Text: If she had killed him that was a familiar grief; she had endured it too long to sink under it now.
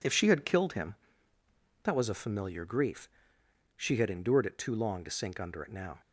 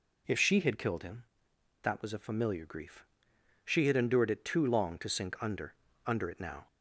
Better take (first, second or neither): first